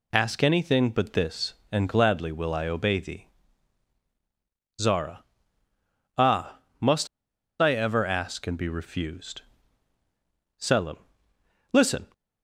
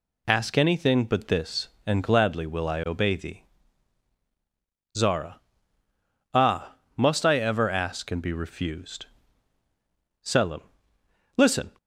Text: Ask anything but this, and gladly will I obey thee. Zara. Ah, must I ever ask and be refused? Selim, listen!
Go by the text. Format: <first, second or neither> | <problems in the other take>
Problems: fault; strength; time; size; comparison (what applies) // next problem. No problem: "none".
second | pauses between "must" and "I"; noticeable; at 7.0 s; 0.53 s long